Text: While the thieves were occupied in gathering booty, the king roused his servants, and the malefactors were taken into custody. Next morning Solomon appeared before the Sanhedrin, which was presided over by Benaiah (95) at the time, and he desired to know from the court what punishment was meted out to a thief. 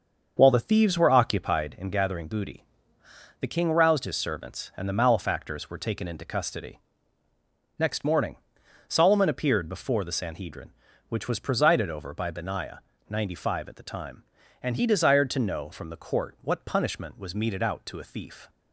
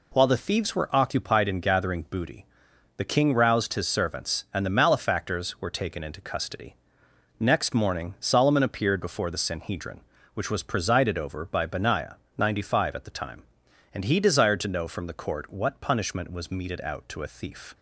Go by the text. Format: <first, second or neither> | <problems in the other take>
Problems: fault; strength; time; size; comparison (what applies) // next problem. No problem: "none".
second | starts louder than the rest; until 1.5 s; 6.5 dB // pauses between "morning" and "Solomon"; noticeable; at 8.3 s; 0.52 s long